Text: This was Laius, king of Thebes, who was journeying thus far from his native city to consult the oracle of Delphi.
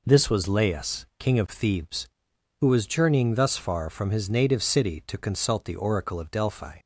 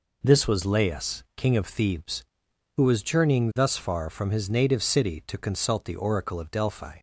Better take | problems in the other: neither | none

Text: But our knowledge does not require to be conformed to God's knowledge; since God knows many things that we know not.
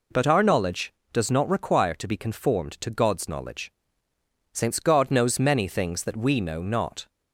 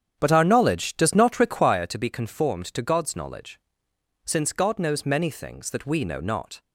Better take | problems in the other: first | starts louder than the rest; strong; until 1.8 s; 8.5 dB

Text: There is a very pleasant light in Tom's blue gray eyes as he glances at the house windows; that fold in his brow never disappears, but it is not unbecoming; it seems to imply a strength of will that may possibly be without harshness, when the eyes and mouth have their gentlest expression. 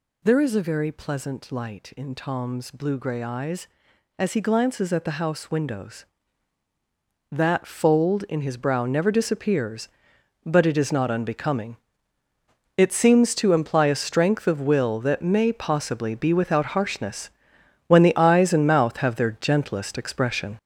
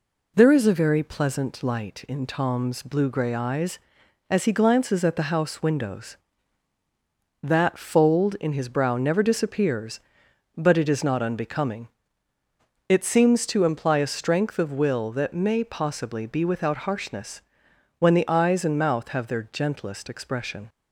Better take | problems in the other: second | gets louder; throughout; 7 dB

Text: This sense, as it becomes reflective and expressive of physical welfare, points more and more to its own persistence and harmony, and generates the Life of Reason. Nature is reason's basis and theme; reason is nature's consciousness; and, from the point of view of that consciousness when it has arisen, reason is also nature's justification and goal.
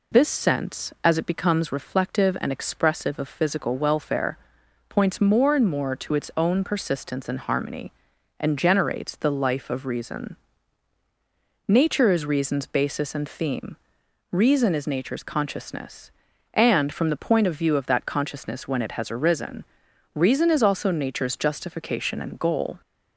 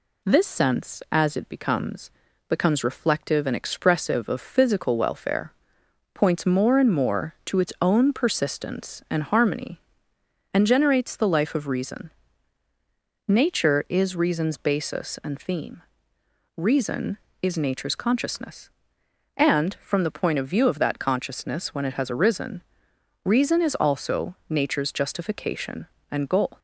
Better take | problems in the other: first | says "becomes" twice; at 2.4 s

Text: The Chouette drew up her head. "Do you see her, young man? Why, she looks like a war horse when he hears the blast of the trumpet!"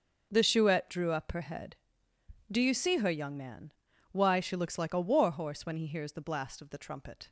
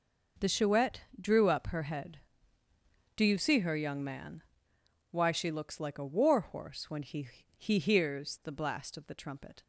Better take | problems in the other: first | pauses between "Chouette" and "drew"; slight; at 1.0 s; 0.18 s long // says "he" twice; at 7.5 s

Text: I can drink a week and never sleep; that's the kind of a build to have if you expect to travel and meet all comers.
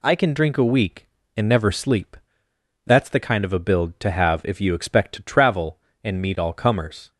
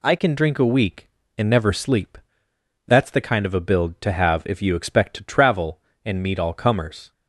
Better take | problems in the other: neither | none

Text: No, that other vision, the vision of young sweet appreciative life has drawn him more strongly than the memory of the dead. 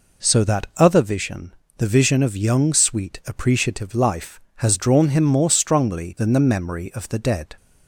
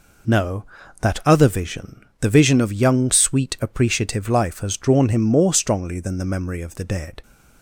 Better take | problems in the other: second | says "So" for "No"; at 0.2 s

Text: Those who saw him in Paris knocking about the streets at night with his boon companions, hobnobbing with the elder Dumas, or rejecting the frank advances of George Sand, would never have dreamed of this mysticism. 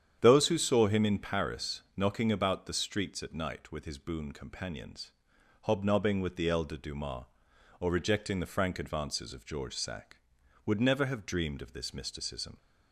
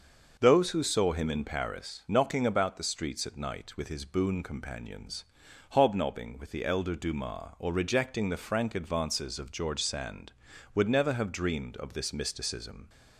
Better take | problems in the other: second | starts louder than the rest; strong; until 1.2 s; 9 dB; also in the second // says "Sack" for "Sand"; at 9.7 s

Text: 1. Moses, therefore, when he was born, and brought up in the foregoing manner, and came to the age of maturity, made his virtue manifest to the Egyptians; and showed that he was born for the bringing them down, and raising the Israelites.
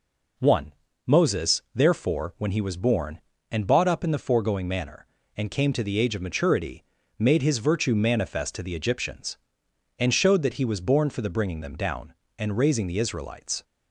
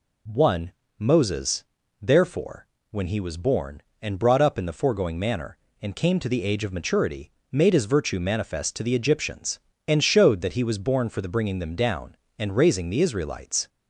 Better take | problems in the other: second | says "bought" for "brought"; at 3.6 s

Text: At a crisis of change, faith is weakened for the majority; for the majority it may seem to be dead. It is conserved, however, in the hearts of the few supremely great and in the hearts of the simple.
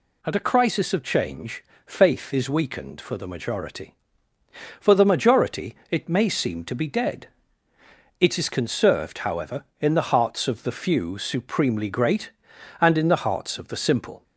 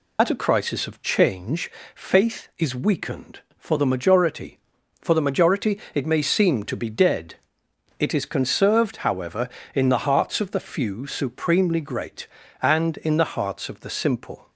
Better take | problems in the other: first | loses the start of "At"; at 0.1 s; 70 ms // pauses between "majority" and "it"; slight; at 5.7 s; 0.16 s long; slight in the first

